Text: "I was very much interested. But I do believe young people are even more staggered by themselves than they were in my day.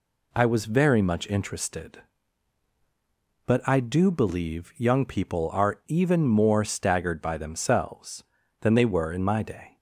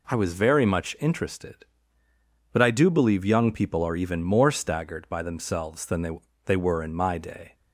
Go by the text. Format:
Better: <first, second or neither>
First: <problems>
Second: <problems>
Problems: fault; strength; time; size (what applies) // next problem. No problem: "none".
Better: first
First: none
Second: says "they" twice; at 6.4 s